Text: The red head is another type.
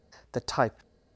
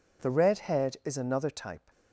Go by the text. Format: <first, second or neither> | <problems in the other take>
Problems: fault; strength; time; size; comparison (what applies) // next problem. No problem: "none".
second | skips "red head is another"; at 0.4 s